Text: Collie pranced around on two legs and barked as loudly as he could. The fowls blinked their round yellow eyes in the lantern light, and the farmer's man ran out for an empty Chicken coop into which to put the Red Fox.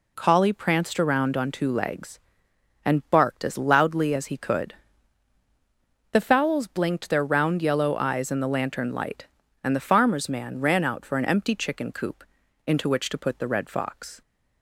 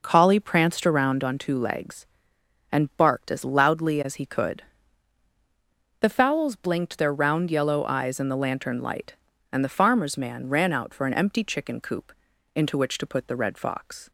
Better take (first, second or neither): first